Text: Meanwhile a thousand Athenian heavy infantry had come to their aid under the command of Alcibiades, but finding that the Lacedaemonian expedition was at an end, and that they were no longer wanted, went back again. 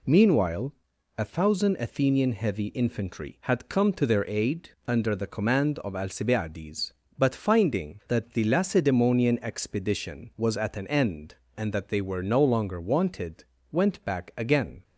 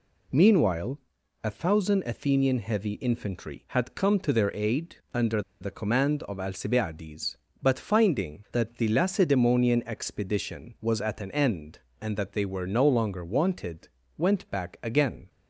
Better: first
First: pauses between "Meanwhile" and "a"; at 0.7 s; 0.42 s long // pauses between "aid" and "under"; slight; at 4.7 s; 0.16 s long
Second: pauses between "Meanwhile" and "a"; at 0.9 s; 0.42 s long // pauses between "aid" and "under"; slight; at 4.9 s; 0.16 s long // pauses between "under" and "the"; slight; at 5.4 s; 0.19 s long

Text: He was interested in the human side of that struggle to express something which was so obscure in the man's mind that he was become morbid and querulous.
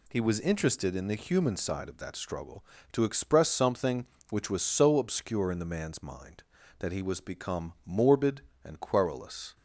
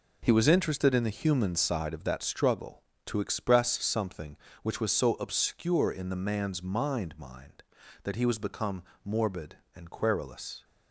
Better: first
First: none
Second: says "mind" twice; at 7.1 s // pauses between "become" and "morbid"; slight; at 8.8 s; 0.20 s long

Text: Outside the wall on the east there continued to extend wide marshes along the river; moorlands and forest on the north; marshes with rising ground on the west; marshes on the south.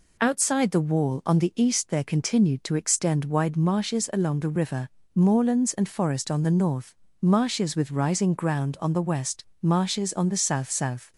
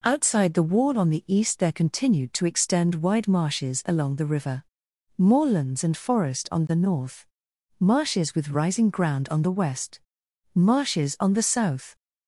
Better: second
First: says "south" twice; at 10.7 s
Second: none

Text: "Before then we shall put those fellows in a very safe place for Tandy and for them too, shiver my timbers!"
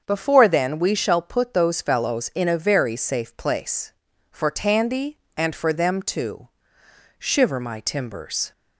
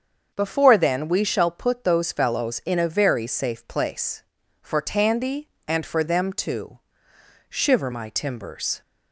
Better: neither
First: starts louder than the rest; until 1.0 s; 7 dB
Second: starts louder than the rest; until 1.3 s; 7 dB

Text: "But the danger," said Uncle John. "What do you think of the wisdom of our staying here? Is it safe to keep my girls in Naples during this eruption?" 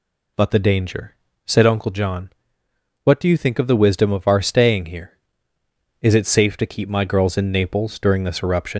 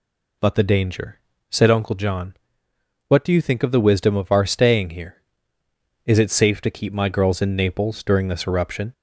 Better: second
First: leaves "eruption" unfinished; at 8.7 s; 95 ms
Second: none

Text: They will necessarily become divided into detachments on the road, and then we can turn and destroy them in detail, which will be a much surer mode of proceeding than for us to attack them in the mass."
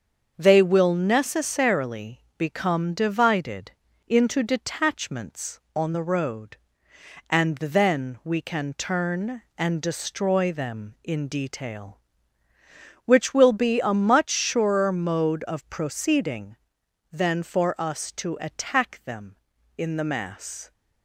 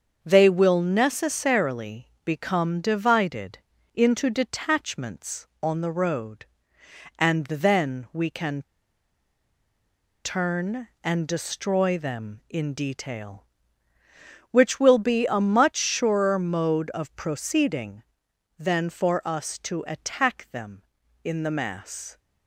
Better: first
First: starts louder than the rest; until 1.3 s; 6.5 dB // pauses between "necessarily" and "become"; slight; at 2.2 s; 0.16 s long // pauses between "divided" and "into"; at 3.7 s; 0.38 s long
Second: starts louder than the rest; until 1.2 s; 6.5 dB // pauses between "necessarily" and "become"; slight; at 2.0 s; 0.16 s long // pauses between "divided" and "into"; at 3.5 s; 0.38 s long // pauses between "can" and "turn"; strong; at 8.6 s; 1.6 s long

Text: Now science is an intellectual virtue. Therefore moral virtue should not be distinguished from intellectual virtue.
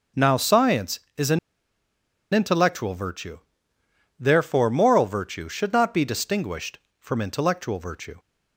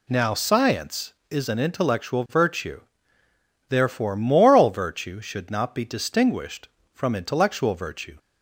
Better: second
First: starts louder than the rest; until 1.3 s; 6.5 dB // pauses between "an" and "intellectual"; noticeable; at 1.3 s; 0.95 s long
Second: none

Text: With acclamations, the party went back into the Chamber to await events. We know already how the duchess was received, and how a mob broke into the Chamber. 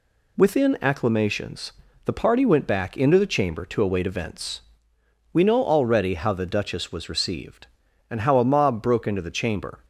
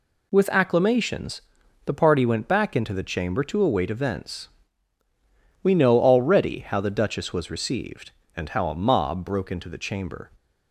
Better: second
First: says "Within" for "With"; at 0.3 s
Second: none

